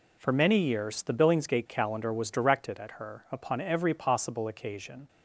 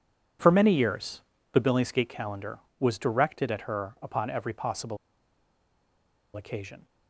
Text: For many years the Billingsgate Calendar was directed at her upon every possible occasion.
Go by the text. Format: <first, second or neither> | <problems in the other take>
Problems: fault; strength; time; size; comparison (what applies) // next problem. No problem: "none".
first | pauses between "years" and "the"; slight; at 1.2 s; 0.32 s long // pauses between "possible" and "occasion"; strong; at 4.9 s; 1.3 s long